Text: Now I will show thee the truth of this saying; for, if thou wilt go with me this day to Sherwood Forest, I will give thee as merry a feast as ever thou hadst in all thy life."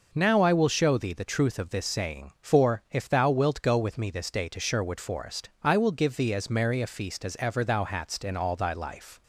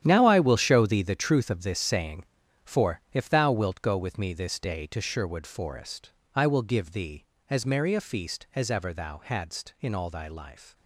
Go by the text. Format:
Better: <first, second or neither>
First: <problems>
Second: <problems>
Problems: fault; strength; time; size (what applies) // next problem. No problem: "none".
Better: first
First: none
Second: gets quieter; strong; throughout; 13 dB